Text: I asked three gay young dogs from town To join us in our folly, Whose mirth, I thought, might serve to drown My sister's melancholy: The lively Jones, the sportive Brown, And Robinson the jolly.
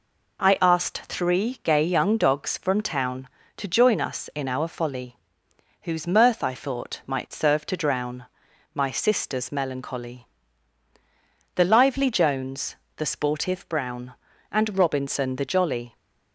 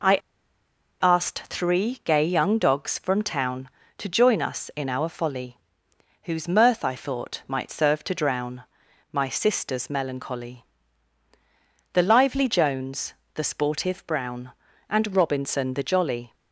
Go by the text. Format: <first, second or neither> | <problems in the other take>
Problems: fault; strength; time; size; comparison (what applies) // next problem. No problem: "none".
first | pauses between "I" and "asked"; noticeable; at 0.1 s; 0.85 s long // pauses between "drown" and "My"; noticeable; at 8.6 s; 0.48 s long; noticeable in the first